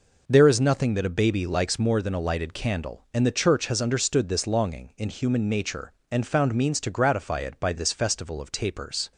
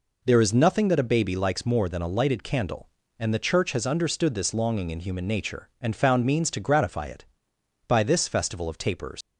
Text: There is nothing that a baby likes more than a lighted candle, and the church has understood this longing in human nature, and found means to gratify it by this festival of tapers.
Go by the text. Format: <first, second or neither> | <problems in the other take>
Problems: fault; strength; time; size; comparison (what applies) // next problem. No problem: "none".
first | leaves "tapers" unfinished; at 9.2 s; 115 ms